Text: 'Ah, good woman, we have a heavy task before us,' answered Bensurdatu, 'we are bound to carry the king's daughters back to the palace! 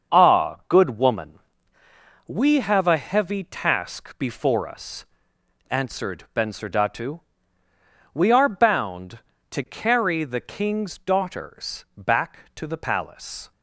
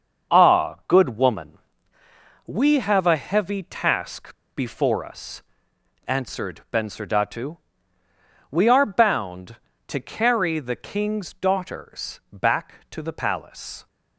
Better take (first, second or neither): first